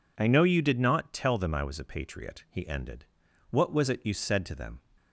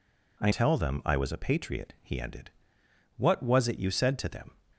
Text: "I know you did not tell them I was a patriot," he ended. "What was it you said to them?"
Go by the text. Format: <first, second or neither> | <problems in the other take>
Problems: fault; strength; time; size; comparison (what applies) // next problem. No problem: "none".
first | skips "know you did not"; at 0.5 s